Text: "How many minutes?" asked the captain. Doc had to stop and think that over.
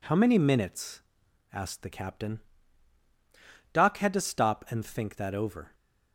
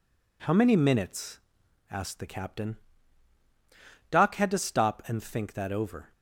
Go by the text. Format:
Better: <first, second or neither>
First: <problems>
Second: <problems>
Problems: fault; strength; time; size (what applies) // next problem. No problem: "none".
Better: neither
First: none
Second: none